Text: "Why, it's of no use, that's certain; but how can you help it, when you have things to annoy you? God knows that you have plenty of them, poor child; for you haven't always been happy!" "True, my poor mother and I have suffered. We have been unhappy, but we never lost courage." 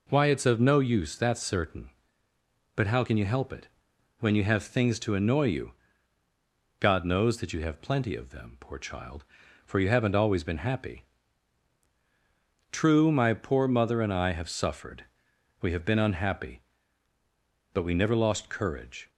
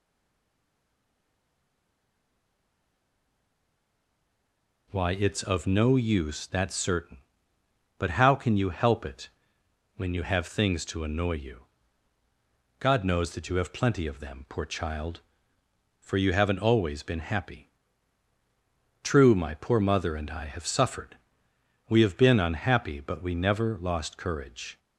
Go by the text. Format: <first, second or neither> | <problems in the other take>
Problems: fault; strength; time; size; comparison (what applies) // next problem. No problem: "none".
first | stays silent before the first word; strong; until 4.8 s; 4.8 s long